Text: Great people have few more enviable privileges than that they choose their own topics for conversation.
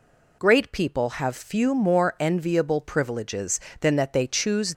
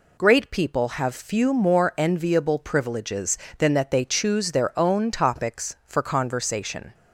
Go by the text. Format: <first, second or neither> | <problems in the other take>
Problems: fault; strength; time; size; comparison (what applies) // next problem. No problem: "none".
second | stops before "their own topics for conversation"; at 4.7 s